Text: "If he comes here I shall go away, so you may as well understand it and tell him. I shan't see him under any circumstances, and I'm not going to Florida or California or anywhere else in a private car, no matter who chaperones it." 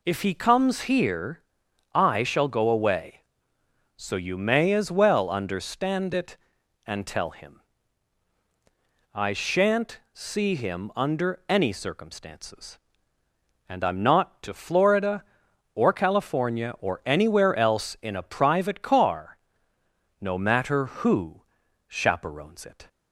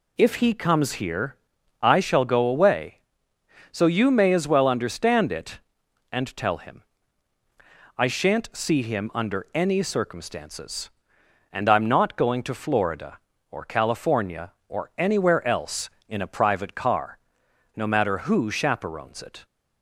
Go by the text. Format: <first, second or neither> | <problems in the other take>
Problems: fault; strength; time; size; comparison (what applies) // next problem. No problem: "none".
second | pauses between "here" and "I"; noticeable; at 1.4 s; 0.52 s long; also in the second // skips "going"; at 14.4 s // pauses between "who" and "chaperones"; at 21.4 s; 0.44 s long